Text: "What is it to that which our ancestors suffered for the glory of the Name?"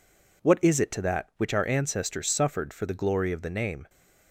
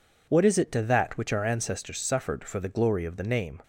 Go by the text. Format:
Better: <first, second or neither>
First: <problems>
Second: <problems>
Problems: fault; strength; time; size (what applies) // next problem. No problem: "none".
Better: neither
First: none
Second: none